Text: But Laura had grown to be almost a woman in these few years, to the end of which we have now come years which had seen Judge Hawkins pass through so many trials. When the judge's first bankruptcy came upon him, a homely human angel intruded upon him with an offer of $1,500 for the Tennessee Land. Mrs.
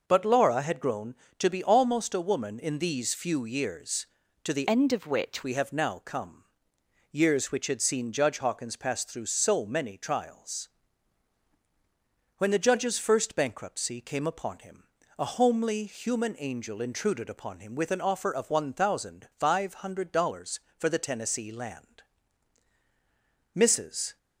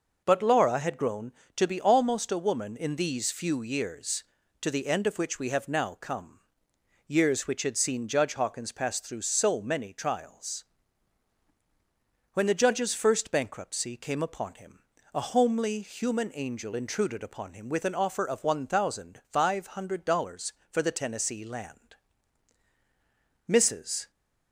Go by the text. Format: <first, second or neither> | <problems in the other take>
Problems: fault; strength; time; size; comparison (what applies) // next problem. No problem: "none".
second | changes voice from "end" to "which"; from 4.6 to 5.4 s; 0.8 s long // pauses between "come" and "years"; noticeable; at 6.4 s; 0.66 s long; noticeable in the second